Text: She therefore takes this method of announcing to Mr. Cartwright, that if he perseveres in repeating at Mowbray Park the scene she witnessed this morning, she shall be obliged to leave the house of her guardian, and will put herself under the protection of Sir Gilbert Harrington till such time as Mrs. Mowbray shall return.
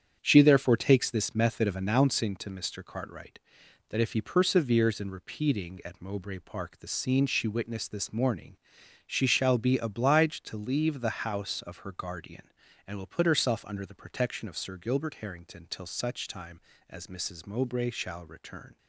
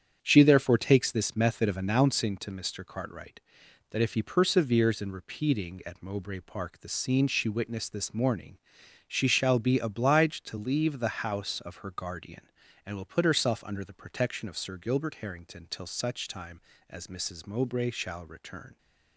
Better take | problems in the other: neither | starts louder than the rest; strong; the same in both

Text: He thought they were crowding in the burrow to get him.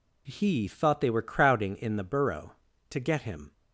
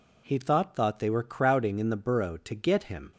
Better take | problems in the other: first | says "thought" twice; at 0.7 s

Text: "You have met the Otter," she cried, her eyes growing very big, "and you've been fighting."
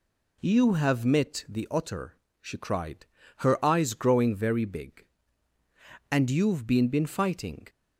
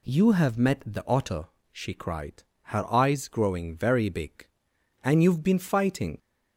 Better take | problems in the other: second | says "been" twice; at 6.8 s

